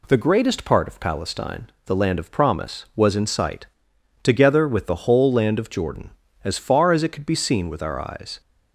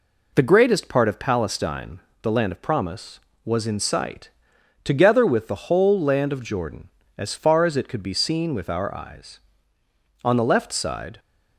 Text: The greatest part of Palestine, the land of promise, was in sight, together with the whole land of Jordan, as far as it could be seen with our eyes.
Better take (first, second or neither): first